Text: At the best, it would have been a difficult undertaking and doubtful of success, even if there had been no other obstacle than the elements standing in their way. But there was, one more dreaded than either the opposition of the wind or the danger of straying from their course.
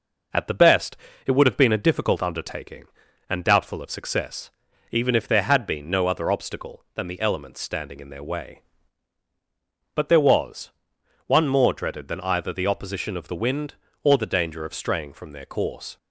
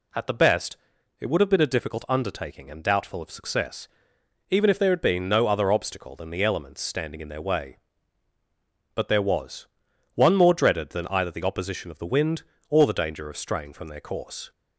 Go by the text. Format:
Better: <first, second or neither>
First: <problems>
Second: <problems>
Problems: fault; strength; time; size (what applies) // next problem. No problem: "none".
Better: neither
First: none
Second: none